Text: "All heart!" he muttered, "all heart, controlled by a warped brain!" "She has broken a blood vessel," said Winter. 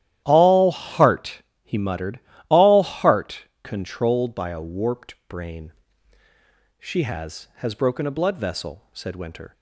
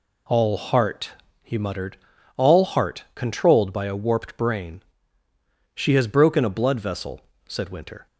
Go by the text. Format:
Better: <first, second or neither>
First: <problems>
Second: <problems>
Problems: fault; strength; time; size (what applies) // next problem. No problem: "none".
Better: second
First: starts louder than the rest; strong; until 1.2 s; 12 dB // says "has" twice; at 7.5 s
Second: none